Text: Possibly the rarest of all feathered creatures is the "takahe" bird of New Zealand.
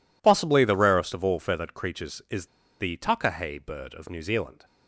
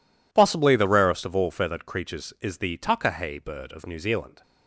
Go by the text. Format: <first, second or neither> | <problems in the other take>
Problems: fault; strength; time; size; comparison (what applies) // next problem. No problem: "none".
second | pauses between "is" and "the"; slight; at 2.4 s; 0.32 s long